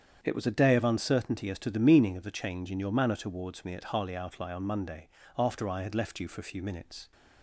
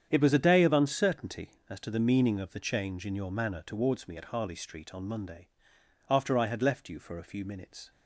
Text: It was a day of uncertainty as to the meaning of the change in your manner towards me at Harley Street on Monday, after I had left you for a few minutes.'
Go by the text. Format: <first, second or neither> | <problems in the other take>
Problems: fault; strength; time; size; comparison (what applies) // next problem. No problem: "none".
second | starts louder than the rest; strong; until 1.2 s; 8 dB; strong in the second // says "Outlie" for "Street"; at 4.1 s